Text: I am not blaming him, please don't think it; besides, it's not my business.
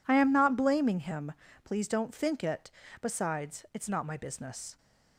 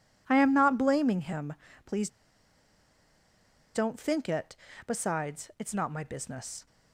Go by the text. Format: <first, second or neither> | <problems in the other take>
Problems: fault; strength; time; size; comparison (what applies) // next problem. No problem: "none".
first | pauses between "please" and "don't"; strong; at 2.0 s; 1.6 s long